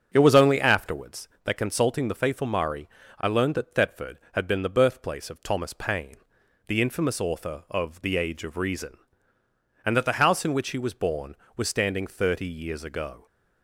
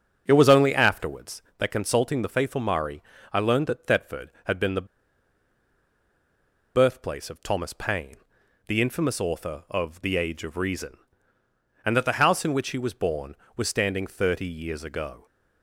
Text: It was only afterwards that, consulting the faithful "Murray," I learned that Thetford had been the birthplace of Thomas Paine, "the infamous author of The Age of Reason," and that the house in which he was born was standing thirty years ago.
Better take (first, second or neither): first